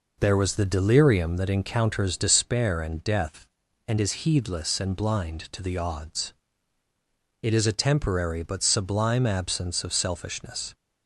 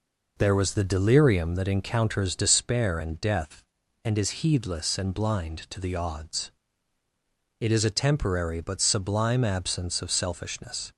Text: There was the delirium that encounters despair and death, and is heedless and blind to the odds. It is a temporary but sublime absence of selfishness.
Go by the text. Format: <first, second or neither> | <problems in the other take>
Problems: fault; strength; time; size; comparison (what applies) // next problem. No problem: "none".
neither | none